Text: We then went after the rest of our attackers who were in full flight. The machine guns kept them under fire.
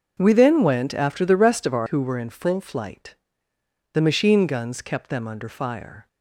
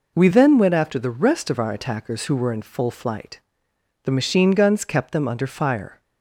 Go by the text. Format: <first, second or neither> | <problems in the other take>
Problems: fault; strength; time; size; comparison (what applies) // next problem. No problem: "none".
second | skips "attackers"; at 1.8 s